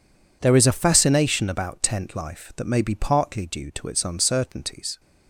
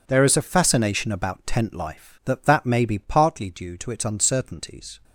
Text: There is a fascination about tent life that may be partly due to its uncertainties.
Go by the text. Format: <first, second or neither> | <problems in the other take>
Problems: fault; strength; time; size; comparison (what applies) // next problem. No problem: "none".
first | says "that" twice; at 2.4 s